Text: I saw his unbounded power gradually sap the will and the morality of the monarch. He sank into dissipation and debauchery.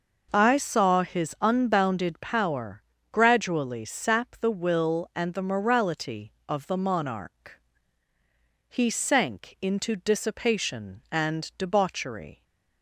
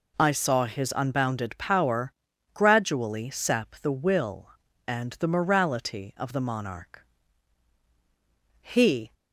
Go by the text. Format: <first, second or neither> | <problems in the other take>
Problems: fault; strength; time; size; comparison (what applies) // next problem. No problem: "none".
first | pauses between "power" and "gradually"; at 2.1 s; 0.40 s long; slight in the first // stops before "sank into dissipation and debauchery"; at 9.1 s